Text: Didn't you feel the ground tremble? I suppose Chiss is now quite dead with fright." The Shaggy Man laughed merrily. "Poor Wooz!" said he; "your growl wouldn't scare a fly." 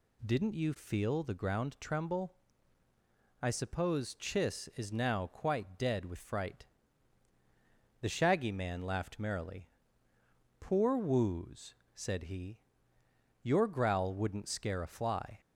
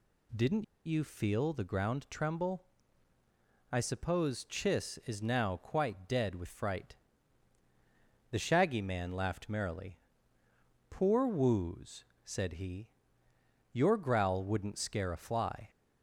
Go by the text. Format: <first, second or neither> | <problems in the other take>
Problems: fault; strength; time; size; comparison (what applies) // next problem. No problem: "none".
first | pauses between "Didn't" and "you"; slight; at 0.6 s; 0.21 s long